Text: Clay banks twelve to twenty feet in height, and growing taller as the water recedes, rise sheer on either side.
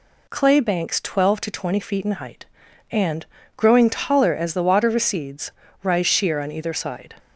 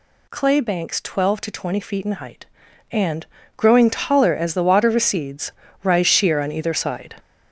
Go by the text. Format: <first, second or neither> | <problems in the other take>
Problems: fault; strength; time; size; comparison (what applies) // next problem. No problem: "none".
first | gets louder; throughout; 6.5 dB // pauses between "and" and "growing"; slight; at 3.2 s; 0.30 s long; slight in the first